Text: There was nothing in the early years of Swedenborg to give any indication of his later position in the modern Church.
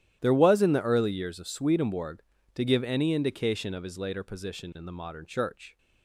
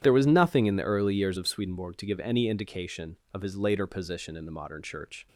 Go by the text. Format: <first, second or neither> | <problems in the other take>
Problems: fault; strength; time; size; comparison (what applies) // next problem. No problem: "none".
second | starts louder than the rest; strong; until 1.2 s; 12.5 dB; strong in the second // skips "nothing"; at 0.6 s